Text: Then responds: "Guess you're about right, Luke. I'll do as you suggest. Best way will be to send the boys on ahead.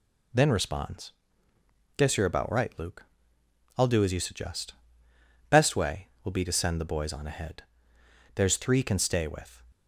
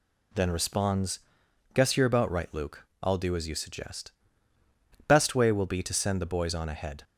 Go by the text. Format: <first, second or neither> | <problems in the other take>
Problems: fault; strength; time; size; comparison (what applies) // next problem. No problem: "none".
second | goes on to say "There's three can stay with"; noticeable; from 8.3 s on; 1.2 s long